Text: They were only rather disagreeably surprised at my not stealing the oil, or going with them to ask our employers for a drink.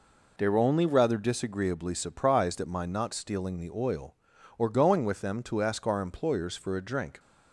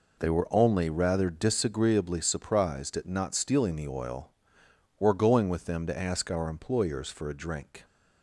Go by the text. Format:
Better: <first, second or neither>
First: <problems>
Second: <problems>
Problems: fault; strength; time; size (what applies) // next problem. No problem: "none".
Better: first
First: none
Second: skips "my"; at 3.0 s